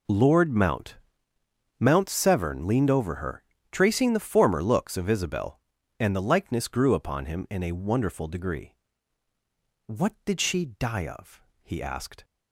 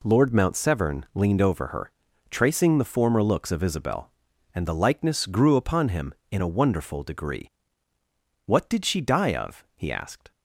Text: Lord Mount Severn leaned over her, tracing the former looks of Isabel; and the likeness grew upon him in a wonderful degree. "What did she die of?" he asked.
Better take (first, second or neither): second